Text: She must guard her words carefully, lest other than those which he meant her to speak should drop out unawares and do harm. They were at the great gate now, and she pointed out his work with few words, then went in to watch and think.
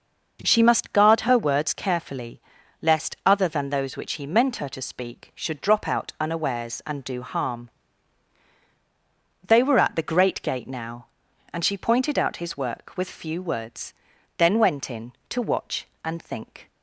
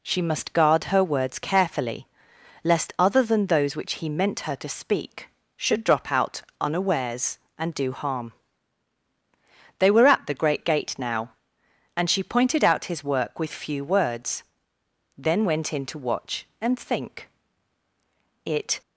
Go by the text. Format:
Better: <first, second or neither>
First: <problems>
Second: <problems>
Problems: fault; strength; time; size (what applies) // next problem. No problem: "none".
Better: first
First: none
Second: pauses between "out" and "unawares"; slight; at 6.4 s; 0.18 s long // goes on to say "It"; slight; from 18.4 s on; 0.36 s long